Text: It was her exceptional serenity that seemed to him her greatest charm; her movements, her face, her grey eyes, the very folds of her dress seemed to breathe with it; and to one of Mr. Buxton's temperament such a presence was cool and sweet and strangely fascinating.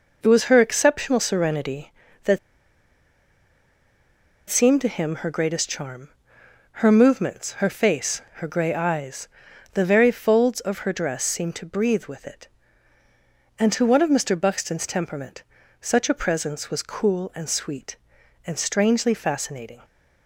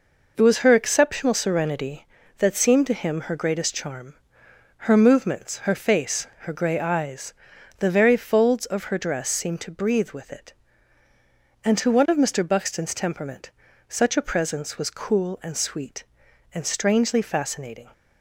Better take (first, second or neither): second